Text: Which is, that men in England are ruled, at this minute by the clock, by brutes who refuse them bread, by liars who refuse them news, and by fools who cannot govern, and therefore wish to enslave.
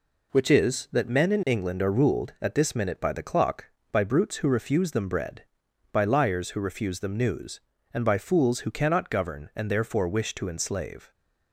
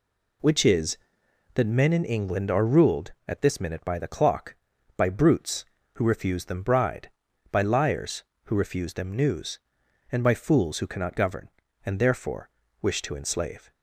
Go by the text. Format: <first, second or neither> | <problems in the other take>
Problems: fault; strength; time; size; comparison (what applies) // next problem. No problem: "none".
first | says "bride" for "bread"; at 6.6 s // pauses between "therefore" and "wish"; slight; at 12.4 s; 0.32 s long